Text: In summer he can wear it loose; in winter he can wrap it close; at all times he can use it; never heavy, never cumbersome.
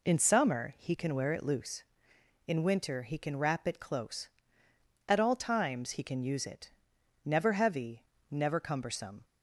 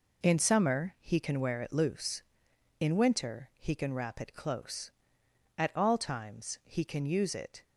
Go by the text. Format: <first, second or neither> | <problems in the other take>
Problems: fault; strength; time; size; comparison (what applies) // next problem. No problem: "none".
first | stops before "never heavy never cumbersome"; at 7.6 s